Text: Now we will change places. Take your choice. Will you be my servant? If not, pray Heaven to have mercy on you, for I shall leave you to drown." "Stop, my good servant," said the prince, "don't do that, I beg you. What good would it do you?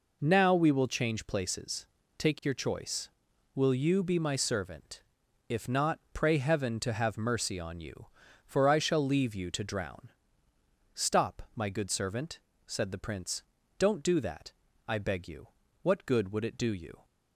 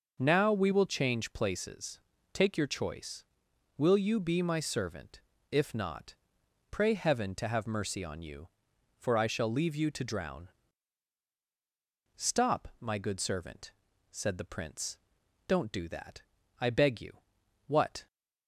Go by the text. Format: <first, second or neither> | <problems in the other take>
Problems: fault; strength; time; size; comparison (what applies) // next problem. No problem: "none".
first | stops before "good would it do you"; at 18.0 s